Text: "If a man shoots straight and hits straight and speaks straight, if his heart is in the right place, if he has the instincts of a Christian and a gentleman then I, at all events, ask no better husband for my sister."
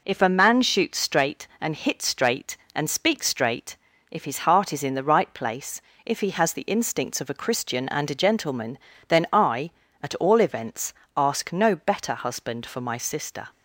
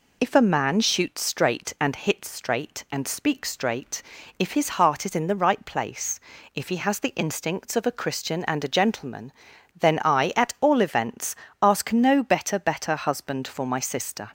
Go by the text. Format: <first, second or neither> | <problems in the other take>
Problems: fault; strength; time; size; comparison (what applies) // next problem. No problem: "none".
first | pauses between "gentleman" and "then"; noticeable; at 9.3 s; 0.48 s long; slight in the first // says "better" twice; at 12.5 s